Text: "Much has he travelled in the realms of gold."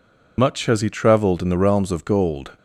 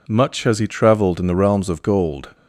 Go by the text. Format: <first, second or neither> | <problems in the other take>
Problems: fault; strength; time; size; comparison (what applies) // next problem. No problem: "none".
second | loses the start of "Much"; at 0.3 s; 80 ms